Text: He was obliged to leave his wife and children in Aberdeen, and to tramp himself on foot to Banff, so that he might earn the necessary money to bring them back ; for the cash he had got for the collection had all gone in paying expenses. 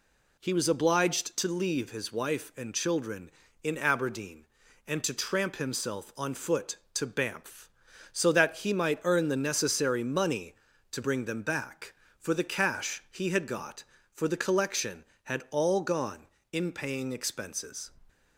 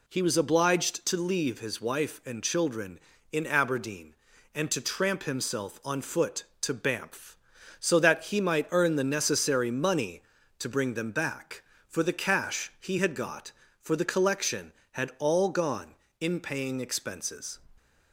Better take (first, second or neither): neither